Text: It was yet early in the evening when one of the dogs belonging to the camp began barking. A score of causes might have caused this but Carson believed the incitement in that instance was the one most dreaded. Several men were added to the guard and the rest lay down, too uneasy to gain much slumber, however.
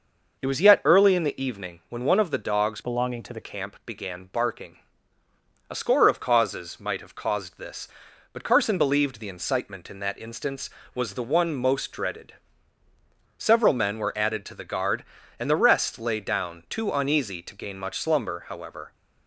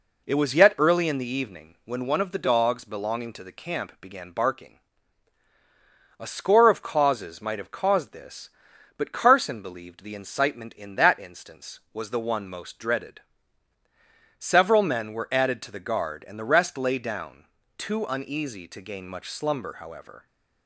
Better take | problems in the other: second | changes voice from "belonging" to "the"; from 2.8 to 3.3 s; 0.5 s long

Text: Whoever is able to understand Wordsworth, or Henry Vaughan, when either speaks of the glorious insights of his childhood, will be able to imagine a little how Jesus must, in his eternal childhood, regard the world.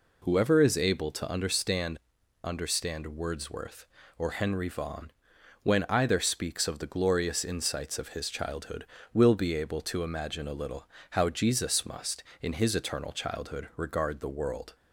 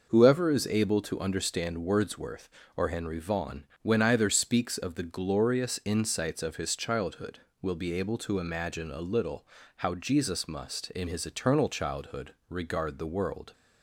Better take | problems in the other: second | says "understand" twice; at 2.4 s // pauses between "little" and "how"; slight; at 10.8 s; 0.24 s long; slight in the second

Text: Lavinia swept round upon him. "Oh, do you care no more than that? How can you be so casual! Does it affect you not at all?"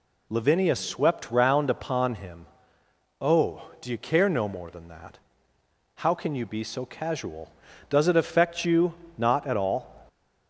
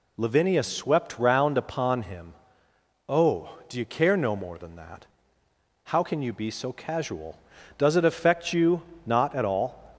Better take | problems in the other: neither | pauses between "you" and "not"; slight; the same in both

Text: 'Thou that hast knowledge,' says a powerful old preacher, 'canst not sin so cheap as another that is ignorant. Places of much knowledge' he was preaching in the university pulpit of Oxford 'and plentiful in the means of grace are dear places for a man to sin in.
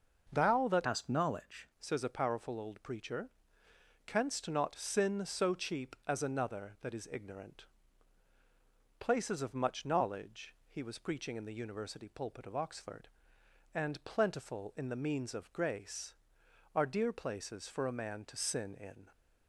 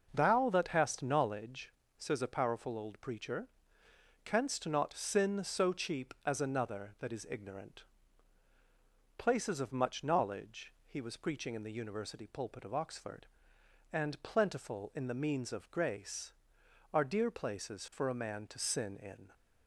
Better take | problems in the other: second | changes voice from "hast" to "knowledge"; from 0.8 to 1.6 s; 0.8 s long

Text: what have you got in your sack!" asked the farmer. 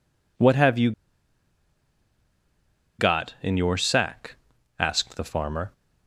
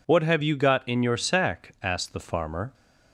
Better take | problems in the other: second | pauses between "you" and "got"; strong; at 0.9 s; 2.0 s long

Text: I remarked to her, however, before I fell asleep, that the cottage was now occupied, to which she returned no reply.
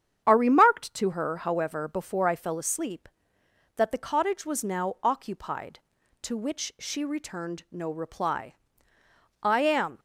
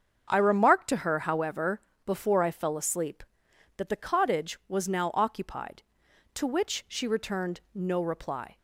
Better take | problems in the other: second | starts louder than the rest; strong; until 1.2 s; 8.5 dB; also in the second // goes on to say "I am"; from 9.4 s on; 0.58 s long

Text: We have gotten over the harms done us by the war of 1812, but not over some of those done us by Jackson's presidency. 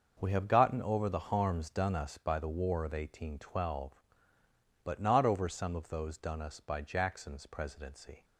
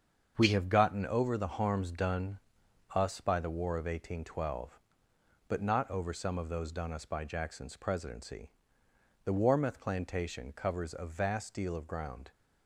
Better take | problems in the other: first | starts louder than the rest; strong; until 1.3 s; 7 dB; also in the first // pauses between "done" and "us"; noticeable; at 2.3 s; 0.54 s long // goes on to say "The Warmouth plantation covers a vast deal of ground"; strong; from 9.2 s on; 3.0 s long

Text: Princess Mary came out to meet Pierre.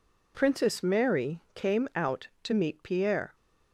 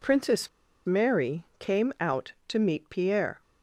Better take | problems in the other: first | pauses between "Princess" and "Mary"; at 0.4 s; 0.38 s long // pauses between "Mary" and "came"; slight; at 1.4 s; 0.16 s long

